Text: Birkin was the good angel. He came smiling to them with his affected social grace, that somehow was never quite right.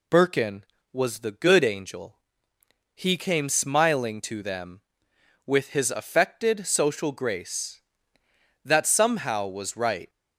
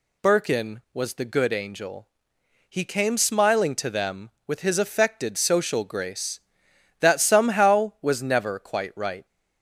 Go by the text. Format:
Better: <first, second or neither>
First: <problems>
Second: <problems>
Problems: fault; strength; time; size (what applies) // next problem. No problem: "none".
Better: second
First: skips "never quite"; at 9.7 s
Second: none